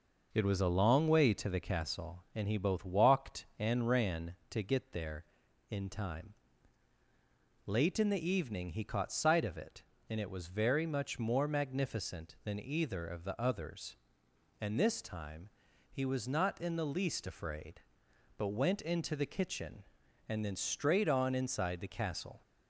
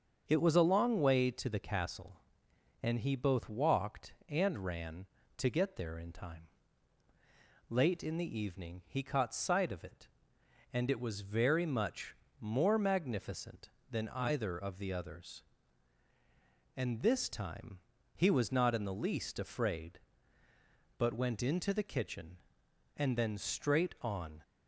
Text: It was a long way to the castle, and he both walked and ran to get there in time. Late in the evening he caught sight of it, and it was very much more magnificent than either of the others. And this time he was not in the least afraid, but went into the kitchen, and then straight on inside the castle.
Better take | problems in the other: first | starts louder than the rest; until 1.2 s; 7 dB // pauses between "much" and "more"; slight; at 12.1 s; 0.24 s long // pauses between "time" and "he"; at 17.7 s; 0.38 s long; also in the first // stops before "inside the castle"; at 24.4 s

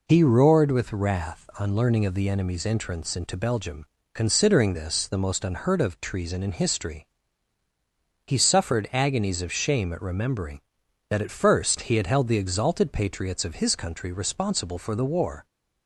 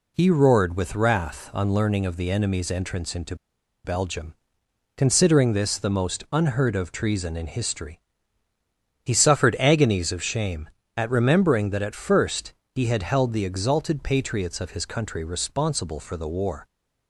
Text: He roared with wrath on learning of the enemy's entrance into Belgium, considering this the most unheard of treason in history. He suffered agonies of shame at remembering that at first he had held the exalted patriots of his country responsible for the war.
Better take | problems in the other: first | pauses between "into" and "Belgium"; noticeable; at 3.3 s; 0.49 s long // pauses between "first" and "he"; slight; at 12.5 s; 0.24 s long

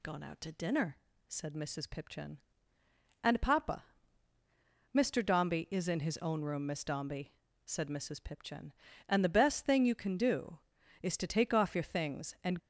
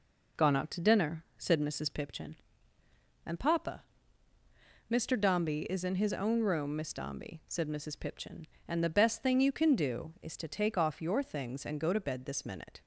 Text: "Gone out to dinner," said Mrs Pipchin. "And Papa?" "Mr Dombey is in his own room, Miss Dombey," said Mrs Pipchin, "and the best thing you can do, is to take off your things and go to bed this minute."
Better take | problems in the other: second | stops before "go to bed this minute"; at 12.5 s

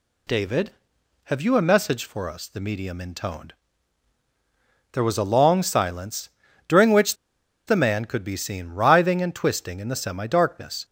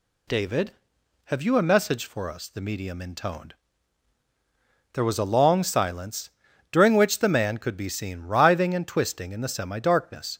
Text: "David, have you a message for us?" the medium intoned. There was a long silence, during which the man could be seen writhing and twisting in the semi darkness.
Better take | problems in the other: second | pauses between "which" and "the"; noticeable; at 7.1 s; 0.51 s long

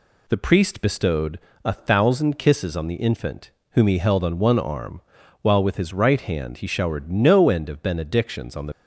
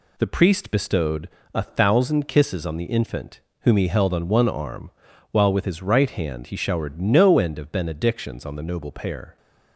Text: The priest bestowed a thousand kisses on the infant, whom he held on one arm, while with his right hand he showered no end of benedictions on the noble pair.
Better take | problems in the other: second | pauses between "bestowed" and "a"; slight; at 1.3 s; 0.24 s long; slight in the second // stops before "noble pair"; at 8.7 s

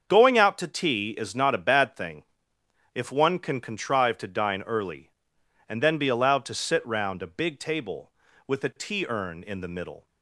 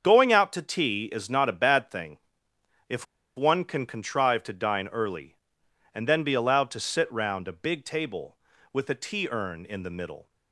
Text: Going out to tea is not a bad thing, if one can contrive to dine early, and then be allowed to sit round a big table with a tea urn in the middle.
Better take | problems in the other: first | starts louder than the rest; until 1.0 s; 7 dB; also in the first // pauses between "if" and "one"; slight; at 3.0 s; 0.32 s long

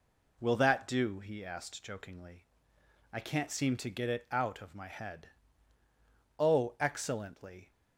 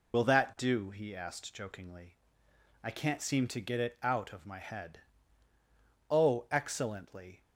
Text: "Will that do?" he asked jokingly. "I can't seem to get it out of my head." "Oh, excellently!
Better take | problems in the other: first | loses the start of "Will"; at 0.1 s; 70 ms

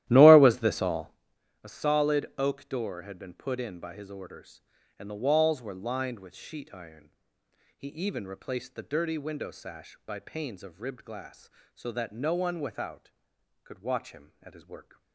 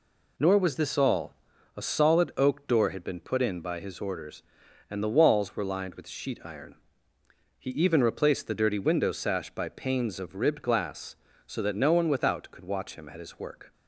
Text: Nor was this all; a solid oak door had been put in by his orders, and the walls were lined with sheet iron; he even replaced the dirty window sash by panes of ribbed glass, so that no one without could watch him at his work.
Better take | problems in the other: second | starts louder than the rest; strong; until 1.2 s; 13.5 dB

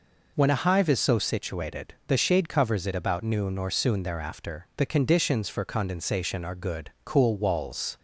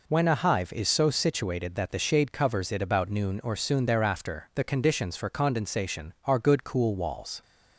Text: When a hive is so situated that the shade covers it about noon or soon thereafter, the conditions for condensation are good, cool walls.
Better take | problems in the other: second | skips "that"; at 2.0 s

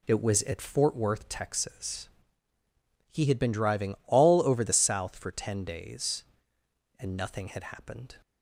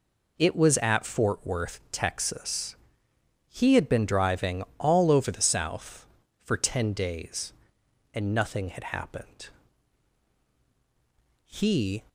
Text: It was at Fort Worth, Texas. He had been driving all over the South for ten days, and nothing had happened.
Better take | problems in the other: first | pauses between "driving" and "all"; slight; at 4.6 s; 0.16 s long // goes on to say "He"; from 11.4 s on; 0.58 s long

